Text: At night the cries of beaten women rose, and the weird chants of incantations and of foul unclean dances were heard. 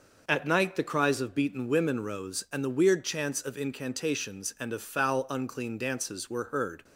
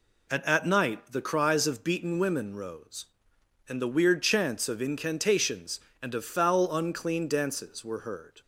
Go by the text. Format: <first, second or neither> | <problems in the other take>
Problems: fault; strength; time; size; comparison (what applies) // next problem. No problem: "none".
first | says "At" twice; at 0.4 s